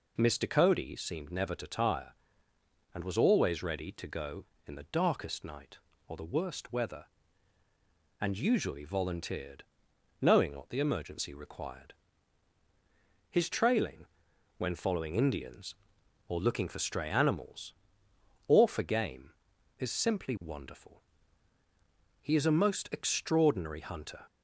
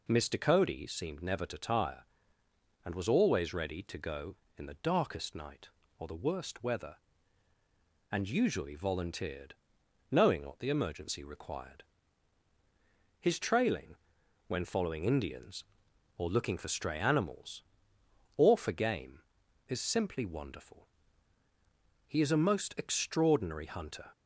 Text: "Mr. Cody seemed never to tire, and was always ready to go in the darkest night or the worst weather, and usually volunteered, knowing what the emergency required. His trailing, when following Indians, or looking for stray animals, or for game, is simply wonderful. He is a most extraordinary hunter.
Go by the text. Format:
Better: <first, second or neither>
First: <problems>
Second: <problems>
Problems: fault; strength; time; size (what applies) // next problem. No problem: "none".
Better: neither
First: none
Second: none